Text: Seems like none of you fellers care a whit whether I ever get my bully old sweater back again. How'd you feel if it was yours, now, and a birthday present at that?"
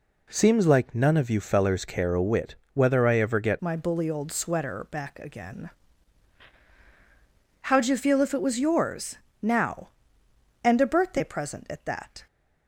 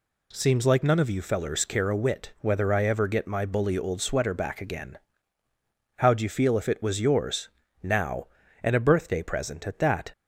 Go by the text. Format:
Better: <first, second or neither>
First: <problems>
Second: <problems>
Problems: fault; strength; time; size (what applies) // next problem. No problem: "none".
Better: second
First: pauses between "whit" and "whether"; slight; at 2.5 s; 0.20 s long // changes voice at "my"; from 3.6 s on; 8.6 s long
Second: none